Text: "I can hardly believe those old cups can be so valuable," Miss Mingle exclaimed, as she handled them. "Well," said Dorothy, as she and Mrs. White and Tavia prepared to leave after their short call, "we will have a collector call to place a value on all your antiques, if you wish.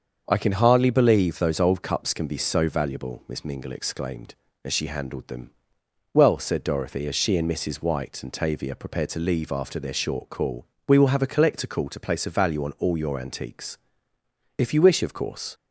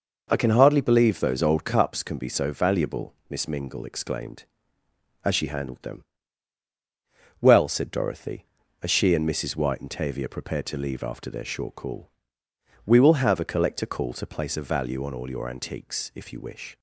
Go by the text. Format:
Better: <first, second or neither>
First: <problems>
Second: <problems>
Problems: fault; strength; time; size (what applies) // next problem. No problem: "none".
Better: second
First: starts louder than the rest; until 1.2 s; 6.5 dB // goes on to say "Of course"; from 15.0 s on; 0.50 s long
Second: none